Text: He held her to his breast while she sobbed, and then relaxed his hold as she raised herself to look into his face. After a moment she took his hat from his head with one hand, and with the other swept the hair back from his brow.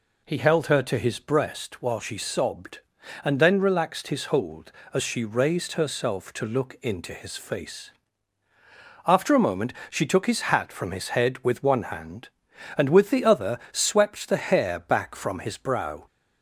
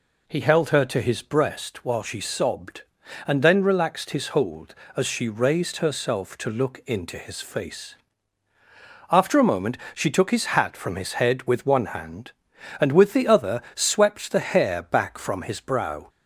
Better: neither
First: pauses between "moment" and "she"; slight; at 9.7 s; 0.16 s long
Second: pauses between "moment" and "she"; slight; at 9.7 s; 0.16 s long

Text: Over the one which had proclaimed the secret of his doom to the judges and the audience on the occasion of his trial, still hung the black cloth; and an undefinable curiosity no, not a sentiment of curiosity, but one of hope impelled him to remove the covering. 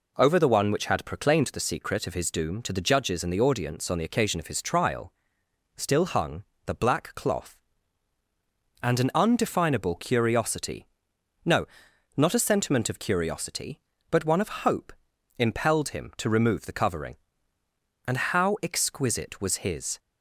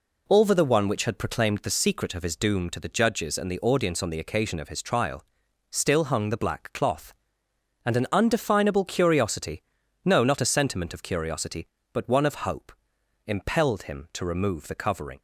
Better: second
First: pauses between "hung" and "the"; slight; at 6.4 s; 0.22 s long // pauses between "curiosity" and "no"; noticeable; at 10.8 s; 0.60 s long // pauses between "hope" and "impelled"; noticeable; at 14.9 s; 0.46 s long // goes on to say "And how exquisite was his"; strong; from 18.0 s on; 1.9 s long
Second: pauses between "curiosity" and "no"; at 9.6 s; 0.42 s long // pauses between "hope" and "impelled"; noticeable; at 12.7 s; 0.56 s long

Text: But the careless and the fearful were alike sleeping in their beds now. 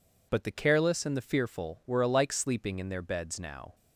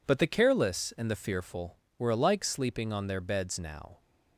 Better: first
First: none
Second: says "on" for "in"; at 2.9 s

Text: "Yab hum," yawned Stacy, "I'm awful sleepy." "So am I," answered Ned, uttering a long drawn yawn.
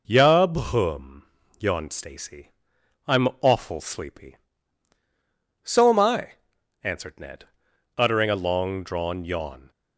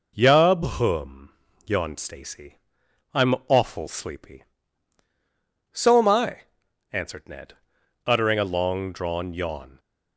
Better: neither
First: none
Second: none

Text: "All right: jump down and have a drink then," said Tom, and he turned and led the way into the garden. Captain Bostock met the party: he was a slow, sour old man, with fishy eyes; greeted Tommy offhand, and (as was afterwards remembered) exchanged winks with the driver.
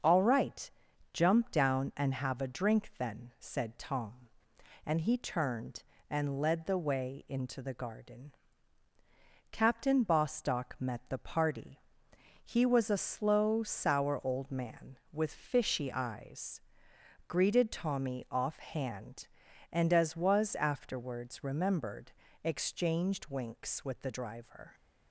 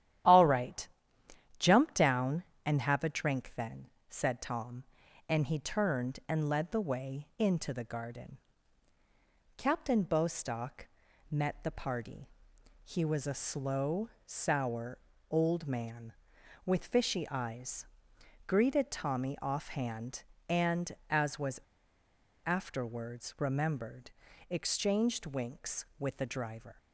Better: first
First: starts louder than the rest; until 1.4 s; 6 dB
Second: starts louder than the rest; strong; until 1.9 s; 11.5 dB // pauses between "Bostock" and "met"; at 10.8 s; 0.42 s long // pauses between "sour" and "old"; slight; at 14.9 s; 0.32 s long // pauses between "was" and "afterwards"; noticeable; at 21.5 s; 0.86 s long

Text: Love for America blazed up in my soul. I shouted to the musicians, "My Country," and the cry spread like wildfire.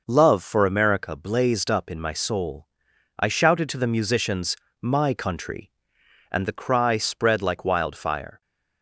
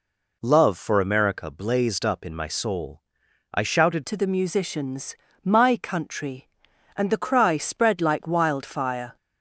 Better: first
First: none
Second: changes voice at "to"; from 4.0 s on; 5.1 s long

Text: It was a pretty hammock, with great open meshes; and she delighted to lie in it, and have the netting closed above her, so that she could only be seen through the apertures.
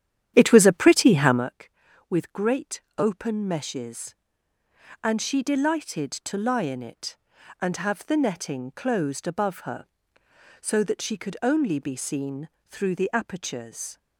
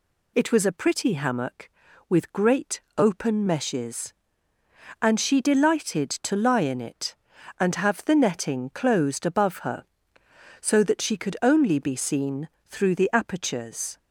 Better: second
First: starts louder than the rest; strong; until 1.5 s; 10.5 dB // pauses between "great" and "open"; slight; at 2.8 s; 0.16 s long // pauses between "seen" and "through"; slight; at 12.4 s; 0.16 s long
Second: pauses between "great" and "open"; slight; at 2.8 s; 0.16 s long // pauses between "seen" and "through"; slight; at 12.4 s; 0.16 s long

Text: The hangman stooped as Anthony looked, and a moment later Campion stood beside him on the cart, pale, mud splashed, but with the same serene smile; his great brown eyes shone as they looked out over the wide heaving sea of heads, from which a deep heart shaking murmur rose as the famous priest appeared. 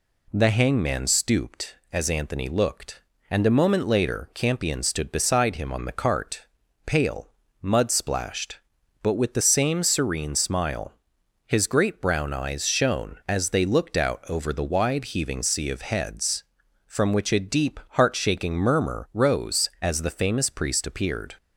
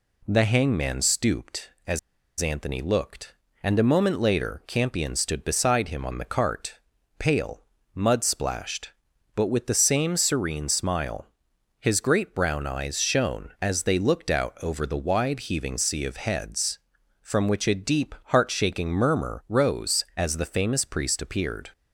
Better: first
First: none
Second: pauses between "as" and "Anthony"; at 1.9 s; 0.40 s long

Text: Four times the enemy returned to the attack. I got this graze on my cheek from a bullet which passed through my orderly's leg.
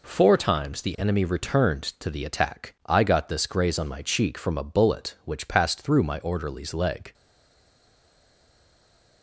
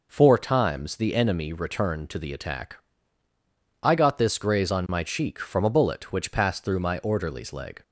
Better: second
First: stays silent after the last word; noticeable; from 7.1 s on; 2.1 s long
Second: none

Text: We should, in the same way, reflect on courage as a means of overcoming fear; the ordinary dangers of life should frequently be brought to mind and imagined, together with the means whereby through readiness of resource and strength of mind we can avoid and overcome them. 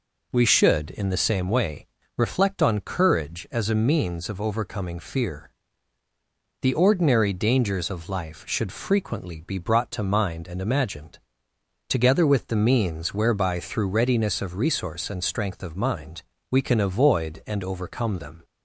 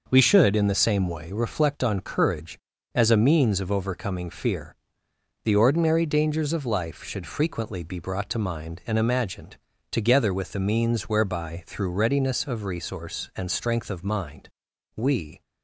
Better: first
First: pauses between "mind" and "we"; slight; at 16.2 s; 0.26 s long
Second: pauses between "mind" and "we"; noticeable; at 14.4 s; 0.46 s long // stops before "can avoid and overcome them"; at 15.4 s

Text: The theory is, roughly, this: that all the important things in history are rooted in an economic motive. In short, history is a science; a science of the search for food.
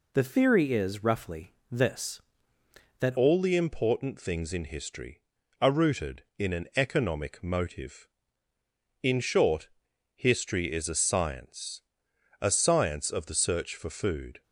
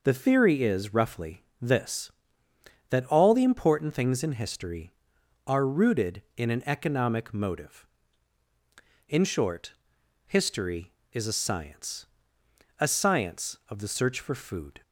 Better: second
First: changes voice at "all"; from 3.1 s on; 11.3 s long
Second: none

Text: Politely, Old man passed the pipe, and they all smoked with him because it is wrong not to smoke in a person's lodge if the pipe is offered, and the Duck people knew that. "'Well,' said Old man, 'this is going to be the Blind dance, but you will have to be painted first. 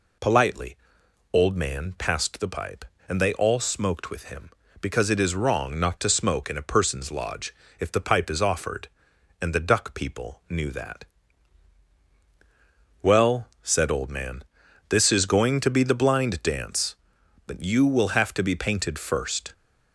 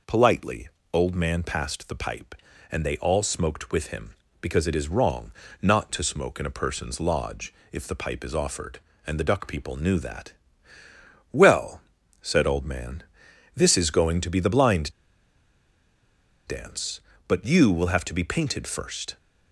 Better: first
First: pauses between "lodge" and "if"; slight; at 7.5 s; 0.24 s long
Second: pauses between "wrong" and "not"; slight; at 5.3 s; 0.32 s long // pauses between "lodge" and "if"; slight; at 7.5 s; 0.16 s long // pauses between "Blind" and "dance"; strong; at 14.9 s; 1.5 s long

